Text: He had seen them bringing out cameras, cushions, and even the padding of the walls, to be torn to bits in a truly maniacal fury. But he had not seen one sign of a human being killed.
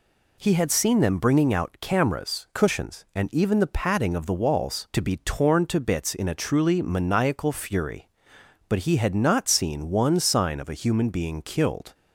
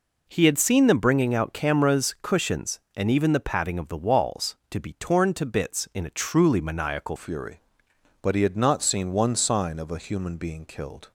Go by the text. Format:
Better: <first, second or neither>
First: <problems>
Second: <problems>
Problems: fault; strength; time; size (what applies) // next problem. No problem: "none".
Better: first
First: none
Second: changes voice at "fury"; from 7.1 s on; 4.0 s long